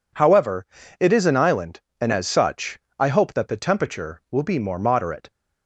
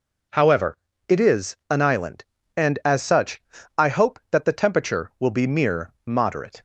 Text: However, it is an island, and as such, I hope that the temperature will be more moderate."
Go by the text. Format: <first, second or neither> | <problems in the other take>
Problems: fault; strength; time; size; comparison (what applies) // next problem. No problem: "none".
first | says "mere" for "more"; at 5.4 s